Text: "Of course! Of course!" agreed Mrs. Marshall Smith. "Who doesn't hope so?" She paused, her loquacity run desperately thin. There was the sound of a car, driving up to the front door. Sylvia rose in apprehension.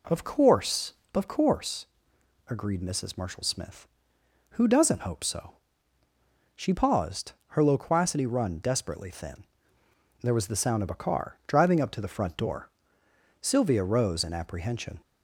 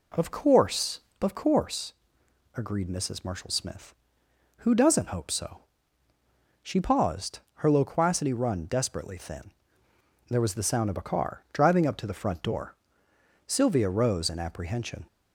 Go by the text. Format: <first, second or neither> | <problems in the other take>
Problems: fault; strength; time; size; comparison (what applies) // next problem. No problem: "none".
neither | none